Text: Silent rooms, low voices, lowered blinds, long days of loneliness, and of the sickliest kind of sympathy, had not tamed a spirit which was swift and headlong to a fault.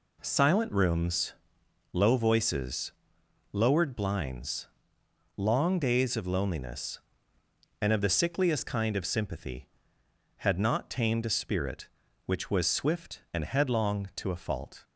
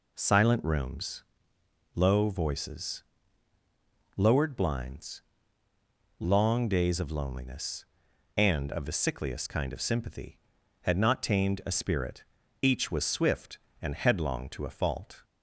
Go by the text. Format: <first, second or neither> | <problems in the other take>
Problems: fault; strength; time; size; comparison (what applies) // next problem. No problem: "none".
first | says "each" for "which"; at 12.6 s